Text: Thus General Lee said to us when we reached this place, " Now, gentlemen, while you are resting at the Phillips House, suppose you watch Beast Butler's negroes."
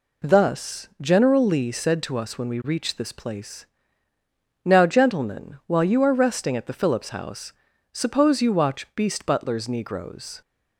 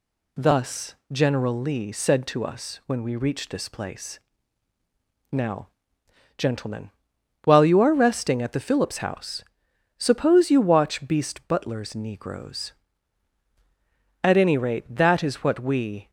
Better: first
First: none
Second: pauses between "Thus" and "General"; slight; at 0.9 s; 0.18 s long // goes on to say "At any rate that is what we"; strong; from 14.2 s on; 1.8 s long

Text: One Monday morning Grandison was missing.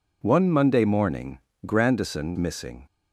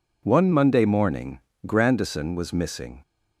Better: second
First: pauses between "morning" and "Grandison"; slight; at 1.4 s; 0.26 s long // skips "was"; at 2.3 s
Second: pauses between "morning" and "Grandison"; slight; at 1.4 s; 0.26 s long

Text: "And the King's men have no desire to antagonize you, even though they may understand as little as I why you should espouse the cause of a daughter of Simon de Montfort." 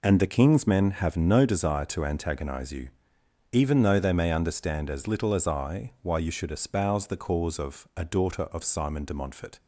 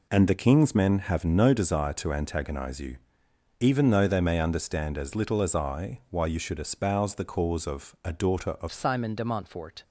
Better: first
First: none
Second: changes voice at "Simon"; from 8.7 s on; 1.1 s long

